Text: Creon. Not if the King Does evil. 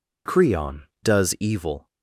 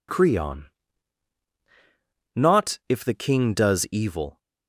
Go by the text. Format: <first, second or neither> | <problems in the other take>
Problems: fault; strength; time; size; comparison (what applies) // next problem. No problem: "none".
second | skips "Not if the King"; at 0.9 s